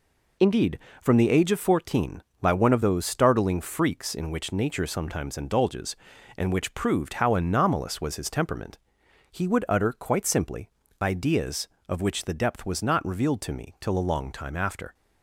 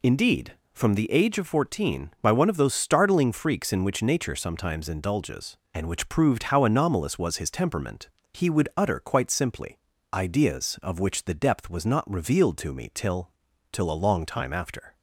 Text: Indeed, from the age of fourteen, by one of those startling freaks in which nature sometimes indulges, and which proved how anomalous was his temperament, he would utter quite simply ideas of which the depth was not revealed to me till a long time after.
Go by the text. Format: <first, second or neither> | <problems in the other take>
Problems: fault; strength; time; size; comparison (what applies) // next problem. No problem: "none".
first | pauses between "simply" and "ideas"; slight; at 9.7 s; 0.34 s long; slight in the first // says "till" twice; at 13.7 s